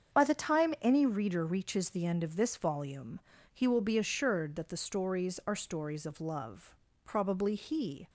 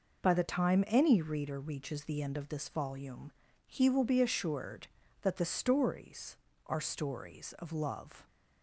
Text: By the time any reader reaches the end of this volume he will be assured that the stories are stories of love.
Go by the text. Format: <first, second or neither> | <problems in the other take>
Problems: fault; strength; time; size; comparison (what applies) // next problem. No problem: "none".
second | starts louder than the rest; strong; until 1.2 s; 7.5 dB // pauses between "volume" and "he"; slight; at 3.2 s; 0.32 s long; slight in the second // goes on to say "Probably he"; noticeable; from 7.0 s on; 1.0 s long